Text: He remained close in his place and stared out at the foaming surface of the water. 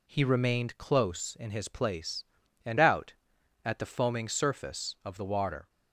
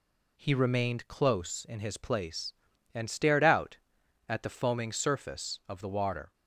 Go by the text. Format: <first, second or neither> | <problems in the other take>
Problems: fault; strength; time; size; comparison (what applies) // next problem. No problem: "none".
second | skips "stared"; at 2.7 s